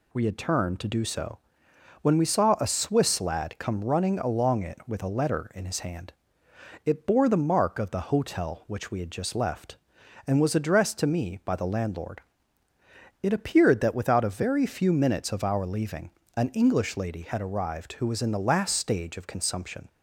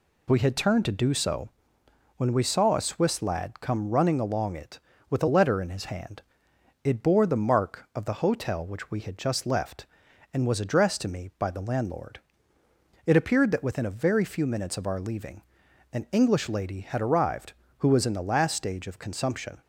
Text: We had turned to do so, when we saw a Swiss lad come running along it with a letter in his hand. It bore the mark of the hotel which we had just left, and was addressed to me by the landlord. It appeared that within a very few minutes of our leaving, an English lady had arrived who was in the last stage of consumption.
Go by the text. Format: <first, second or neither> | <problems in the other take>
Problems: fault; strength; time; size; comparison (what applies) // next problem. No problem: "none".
second | says "without" for "within"; at 13.9 s